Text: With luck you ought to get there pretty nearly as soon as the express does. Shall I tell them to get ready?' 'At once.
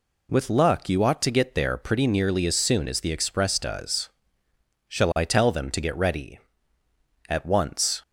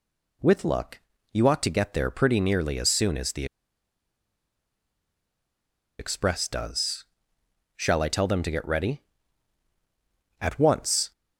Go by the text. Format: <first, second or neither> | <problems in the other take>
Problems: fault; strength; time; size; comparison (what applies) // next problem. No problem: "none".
first | pauses between "luck" and "you"; slight; at 0.9 s; 0.32 s long // pauses between "the" and "express"; strong; at 3.4 s; 2.5 s long